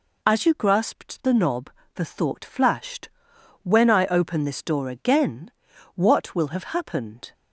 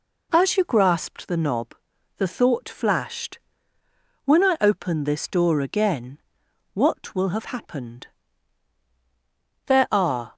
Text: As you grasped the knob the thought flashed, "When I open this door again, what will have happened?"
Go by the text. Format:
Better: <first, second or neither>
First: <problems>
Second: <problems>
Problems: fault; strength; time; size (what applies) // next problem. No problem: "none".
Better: first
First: pauses between "knob" and "the"; slight; at 1.7 s; 0.24 s long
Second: pauses between "knob" and "the"; at 1.7 s; 0.42 s long // goes on to say "There are"; noticeable; from 9.6 s on; 0.68 s long